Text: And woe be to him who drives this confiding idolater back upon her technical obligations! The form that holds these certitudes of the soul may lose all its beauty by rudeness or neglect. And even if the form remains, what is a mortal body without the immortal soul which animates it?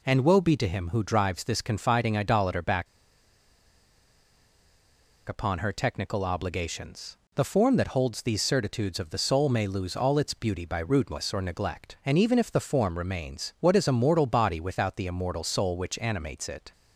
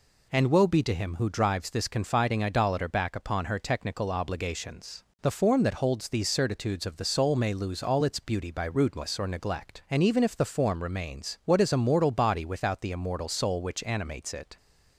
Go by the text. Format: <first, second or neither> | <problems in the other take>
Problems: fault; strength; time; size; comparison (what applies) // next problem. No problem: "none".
second | pauses between "back" and "upon"; strong; at 2.8 s; 2.4 s long